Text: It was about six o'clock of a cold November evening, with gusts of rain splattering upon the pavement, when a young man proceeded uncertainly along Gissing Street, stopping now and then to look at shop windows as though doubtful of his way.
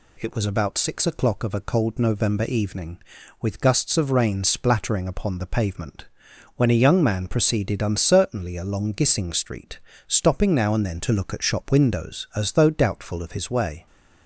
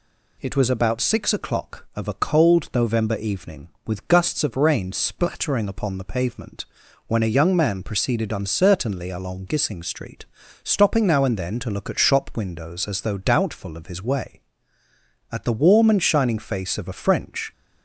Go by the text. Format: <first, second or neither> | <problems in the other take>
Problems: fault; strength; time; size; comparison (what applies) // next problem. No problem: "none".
first | goes on to say "At the warm and shining face of a French"; strong; from 15.2 s on; 2.2 s long